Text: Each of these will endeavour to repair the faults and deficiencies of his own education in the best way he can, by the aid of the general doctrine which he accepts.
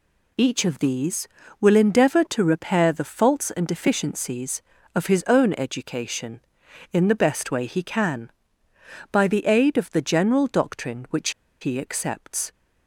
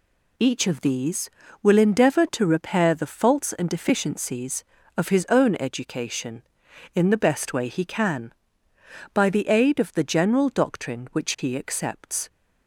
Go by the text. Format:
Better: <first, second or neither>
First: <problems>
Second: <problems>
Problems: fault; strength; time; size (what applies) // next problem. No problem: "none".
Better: second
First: pauses between "which" and "he"; slight; at 11.2 s; 0.31 s long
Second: none